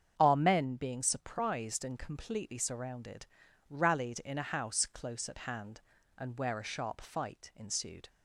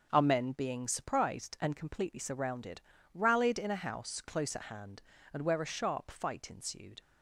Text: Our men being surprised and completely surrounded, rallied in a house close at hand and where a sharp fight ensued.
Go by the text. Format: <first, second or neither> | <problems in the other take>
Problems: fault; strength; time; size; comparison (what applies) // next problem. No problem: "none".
neither | starts louder than the rest; the same in both